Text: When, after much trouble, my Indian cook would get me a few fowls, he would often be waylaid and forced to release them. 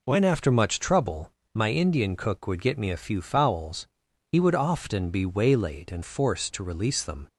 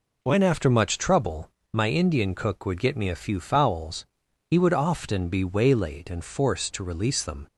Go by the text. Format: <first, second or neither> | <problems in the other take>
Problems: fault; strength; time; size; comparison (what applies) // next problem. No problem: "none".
neither | none